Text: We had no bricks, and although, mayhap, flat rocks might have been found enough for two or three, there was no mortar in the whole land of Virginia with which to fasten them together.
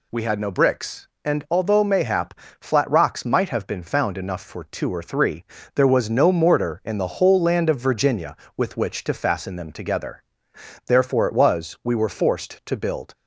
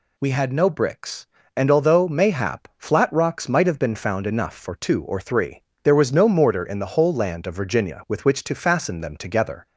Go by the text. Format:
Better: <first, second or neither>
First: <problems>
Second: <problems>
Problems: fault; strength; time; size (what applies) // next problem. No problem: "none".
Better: second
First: goes on to say "Therefore it was we were forced to build"; strong; from 10.8 s on; 2.2 s long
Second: none